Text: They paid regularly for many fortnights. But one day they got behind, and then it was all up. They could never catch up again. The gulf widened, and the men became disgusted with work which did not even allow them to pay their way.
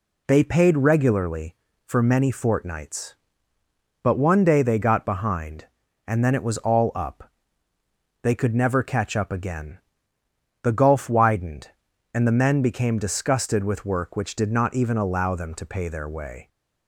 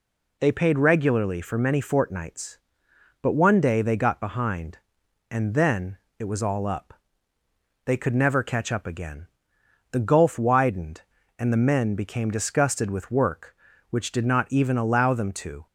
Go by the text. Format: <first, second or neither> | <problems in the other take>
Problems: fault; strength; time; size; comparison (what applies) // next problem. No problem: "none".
first | pauses between "then" and "it"; slight; at 5.9 s; 0.22 s long // stops before "pay their way"; at 15.6 s